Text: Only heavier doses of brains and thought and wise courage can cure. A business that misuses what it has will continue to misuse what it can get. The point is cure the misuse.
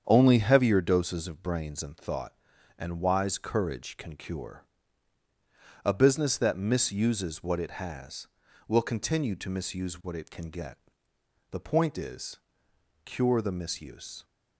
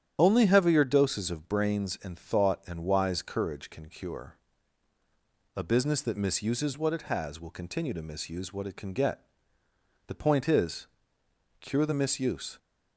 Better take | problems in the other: first | loses the start of "Only"; at 0.1 s; 35 ms // starts louder than the rest; strong; until 1.1 s; 9.5 dB; strong in the first // pauses between "is" and "cure"; noticeable; at 10.8 s; 0.72 s long; noticeable in the first

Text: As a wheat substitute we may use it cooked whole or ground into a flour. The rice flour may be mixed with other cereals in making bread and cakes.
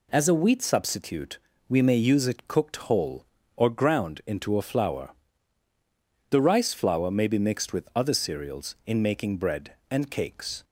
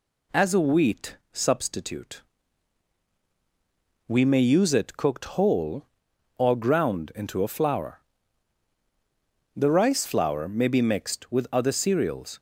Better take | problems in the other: first | pauses between "wheat" and "substitute"; slight; at 1.1 s; 0.16 s long // pauses between "substitute" and "we"; strong; at 2.2 s; 1.8 s long; slight in the first // stops before "in making bread and cakes"; at 12.3 s

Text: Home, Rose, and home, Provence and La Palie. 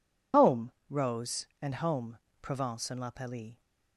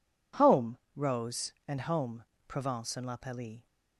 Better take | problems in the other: second | loses the start of "Home"; at 0.3 s; 65 ms

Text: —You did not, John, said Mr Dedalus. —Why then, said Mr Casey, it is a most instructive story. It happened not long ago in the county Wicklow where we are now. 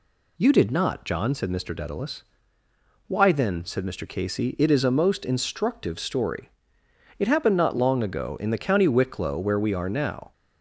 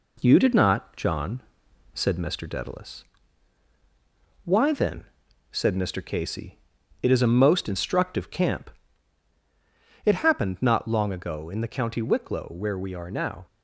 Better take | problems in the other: first | says "camp" for "story"; at 8.2 s

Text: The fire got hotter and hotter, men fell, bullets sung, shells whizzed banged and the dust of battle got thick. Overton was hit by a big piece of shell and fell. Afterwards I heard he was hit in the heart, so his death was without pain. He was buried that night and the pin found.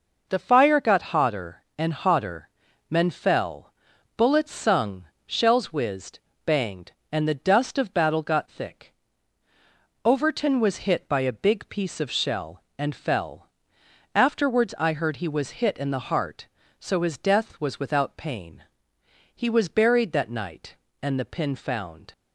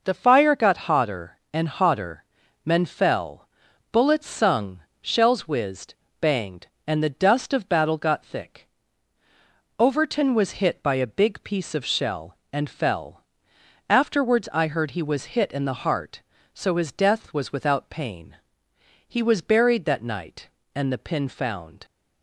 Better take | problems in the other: neither | pauses between "whizzed" and "banged"; slight; the same in both

